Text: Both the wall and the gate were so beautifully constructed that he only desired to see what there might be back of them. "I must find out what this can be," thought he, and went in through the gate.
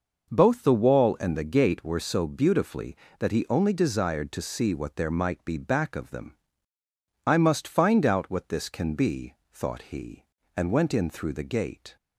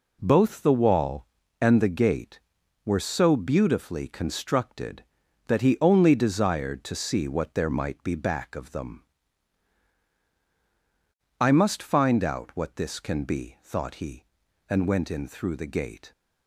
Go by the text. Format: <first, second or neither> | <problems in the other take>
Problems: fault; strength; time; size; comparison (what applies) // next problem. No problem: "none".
second | skips "constructed"; at 3.0 s